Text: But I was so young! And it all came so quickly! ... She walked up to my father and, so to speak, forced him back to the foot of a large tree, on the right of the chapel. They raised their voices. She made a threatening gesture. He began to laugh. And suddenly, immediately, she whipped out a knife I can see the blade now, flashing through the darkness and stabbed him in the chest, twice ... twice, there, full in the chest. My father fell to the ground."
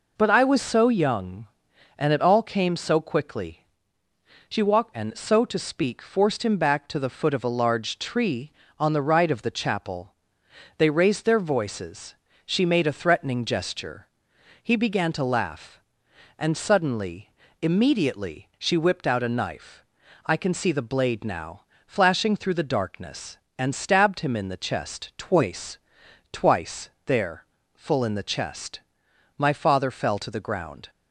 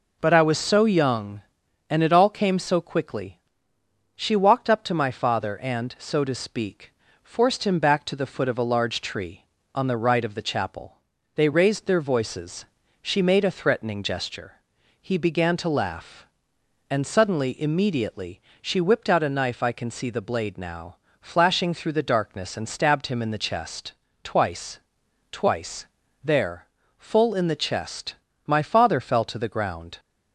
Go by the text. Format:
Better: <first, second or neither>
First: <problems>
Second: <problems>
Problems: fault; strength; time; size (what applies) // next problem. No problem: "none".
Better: second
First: skips "up to my father"; at 4.9 s // pauses between "knife" and "I"; at 19.8 s; 0.42 s long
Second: none